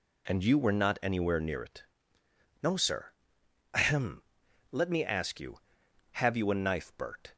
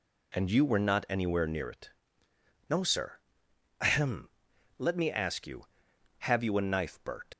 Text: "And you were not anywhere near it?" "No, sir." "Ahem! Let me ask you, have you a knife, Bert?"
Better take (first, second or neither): first